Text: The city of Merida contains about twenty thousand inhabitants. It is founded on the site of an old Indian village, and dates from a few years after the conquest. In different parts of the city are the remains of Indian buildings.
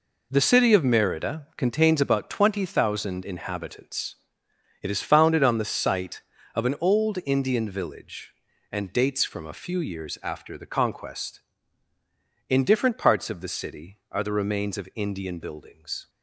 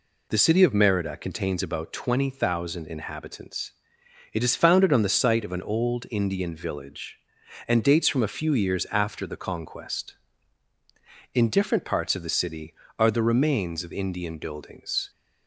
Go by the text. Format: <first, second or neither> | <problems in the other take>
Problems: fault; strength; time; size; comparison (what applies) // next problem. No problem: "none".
neither | none